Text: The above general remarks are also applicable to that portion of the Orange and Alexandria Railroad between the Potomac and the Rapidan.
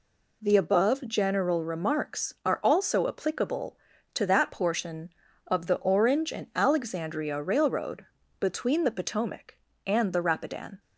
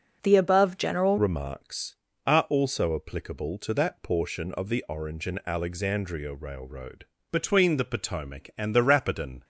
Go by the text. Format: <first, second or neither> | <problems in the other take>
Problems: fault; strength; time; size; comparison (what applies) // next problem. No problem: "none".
first | changes voice at "remarks"; from 1.1 s on; 8.3 s long // pauses between "Railroad" and "between"; slight; at 7.0 s; 0.26 s long; slight in the first